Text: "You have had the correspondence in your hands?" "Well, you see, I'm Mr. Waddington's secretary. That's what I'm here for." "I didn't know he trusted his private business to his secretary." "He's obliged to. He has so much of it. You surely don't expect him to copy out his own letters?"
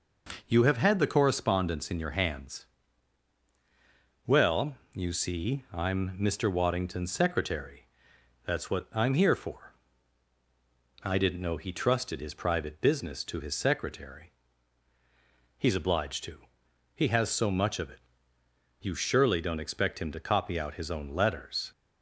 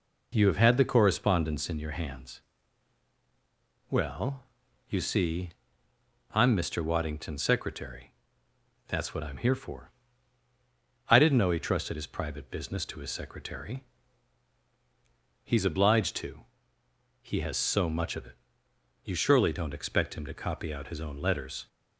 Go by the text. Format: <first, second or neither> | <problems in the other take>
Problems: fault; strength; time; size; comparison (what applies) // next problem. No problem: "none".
neither | none